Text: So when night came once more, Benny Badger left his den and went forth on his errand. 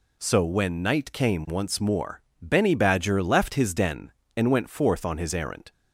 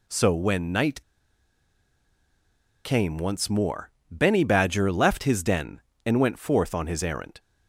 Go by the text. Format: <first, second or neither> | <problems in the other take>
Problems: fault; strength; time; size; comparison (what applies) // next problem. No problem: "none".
first | pauses between "night" and "came"; strong; at 1.0 s; 1.8 s long